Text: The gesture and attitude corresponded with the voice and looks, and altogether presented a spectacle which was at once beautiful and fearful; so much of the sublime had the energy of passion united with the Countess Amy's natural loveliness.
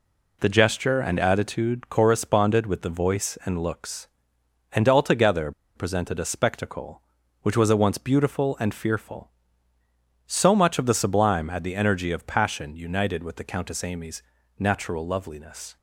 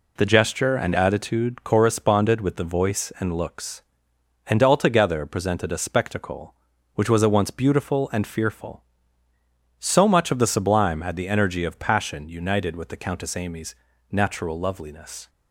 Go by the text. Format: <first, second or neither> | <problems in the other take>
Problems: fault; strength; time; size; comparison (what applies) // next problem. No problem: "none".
second | pauses between "altogether" and "presented"; slight; at 5.5 s; 0.24 s long // pauses between "Amy's" and "natural"; at 14.2 s; 0.38 s long; also in the second